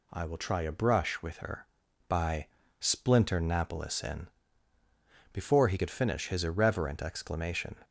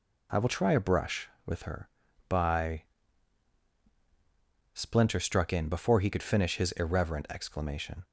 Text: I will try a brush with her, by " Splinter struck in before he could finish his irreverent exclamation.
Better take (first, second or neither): second